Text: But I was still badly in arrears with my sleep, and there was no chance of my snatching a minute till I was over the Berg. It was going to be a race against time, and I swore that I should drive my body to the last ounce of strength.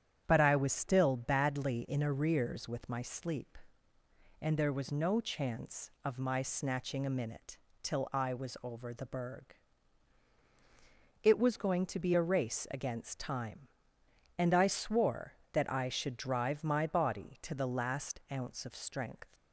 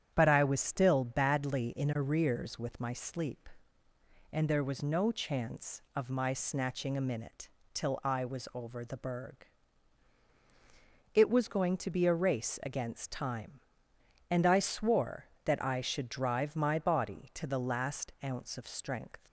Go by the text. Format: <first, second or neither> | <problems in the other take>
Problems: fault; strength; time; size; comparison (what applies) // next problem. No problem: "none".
neither | starts louder than the rest; strong; the same in both // pauses between "minute" and "till"; slight; the same in both